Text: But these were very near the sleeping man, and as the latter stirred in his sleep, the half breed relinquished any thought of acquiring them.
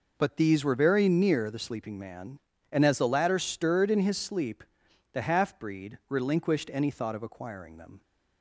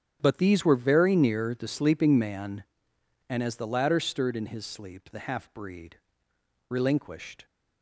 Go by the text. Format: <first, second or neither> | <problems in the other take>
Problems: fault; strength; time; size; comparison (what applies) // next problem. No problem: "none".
first | starts louder than the rest; strong; until 1.2 s; 8.5 dB // pauses between "breed" and "relinquished"; noticeable; at 5.9 s; 0.72 s long // stops before "any thought of acquiring them"; at 7.4 s